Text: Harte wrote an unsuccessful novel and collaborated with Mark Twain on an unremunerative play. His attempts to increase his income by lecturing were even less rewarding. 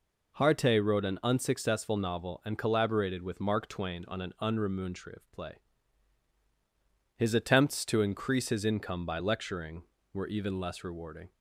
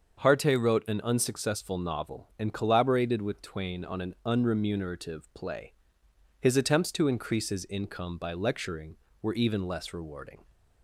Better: first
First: none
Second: starts louder than the rest; until 1.3 s; 6.5 dB // skips "Mark"; at 3.4 s

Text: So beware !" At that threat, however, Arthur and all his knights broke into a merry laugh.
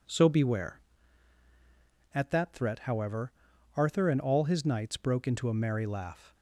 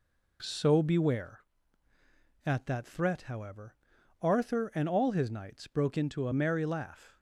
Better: neither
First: none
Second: none

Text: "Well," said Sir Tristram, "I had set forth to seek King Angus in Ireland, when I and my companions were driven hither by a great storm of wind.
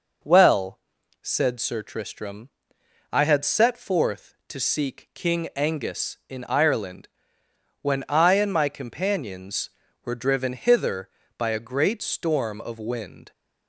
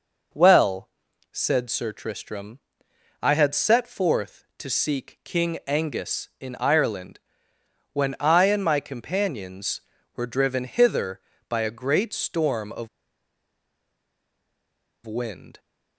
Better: first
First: none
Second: pauses between "of" and "wind"; strong; at 12.8 s; 2.1 s long

